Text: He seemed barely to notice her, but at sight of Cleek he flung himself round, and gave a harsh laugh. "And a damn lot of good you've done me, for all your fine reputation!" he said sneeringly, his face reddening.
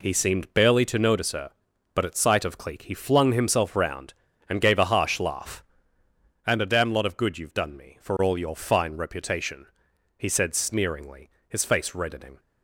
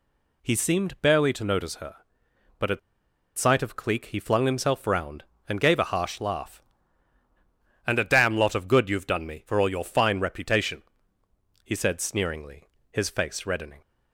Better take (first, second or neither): first